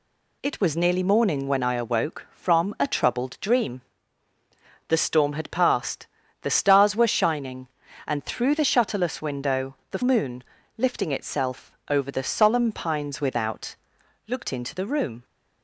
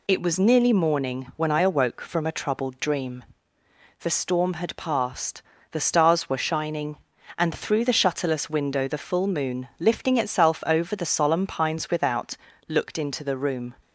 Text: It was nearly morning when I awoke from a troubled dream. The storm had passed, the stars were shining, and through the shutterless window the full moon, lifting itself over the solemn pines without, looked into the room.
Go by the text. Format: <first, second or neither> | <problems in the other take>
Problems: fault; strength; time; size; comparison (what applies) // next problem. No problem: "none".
second | skips "full"; at 10.0 s // pauses between "itself" and "over"; slight; at 11.7 s; 0.16 s long